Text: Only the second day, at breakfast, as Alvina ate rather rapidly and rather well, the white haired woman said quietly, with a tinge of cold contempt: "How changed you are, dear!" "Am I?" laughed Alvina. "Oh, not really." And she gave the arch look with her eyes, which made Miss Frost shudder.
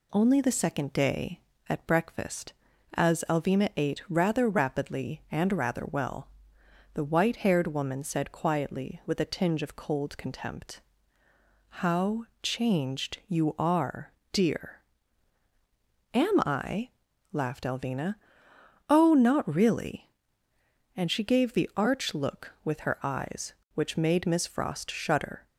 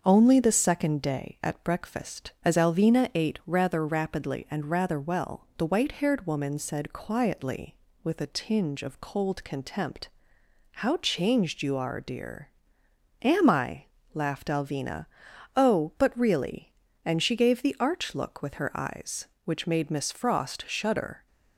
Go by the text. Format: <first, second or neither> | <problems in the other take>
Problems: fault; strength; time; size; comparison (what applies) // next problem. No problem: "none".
first | starts louder than the rest; until 1.0 s; 6.5 dB // says "but" for "not"; at 15.9 s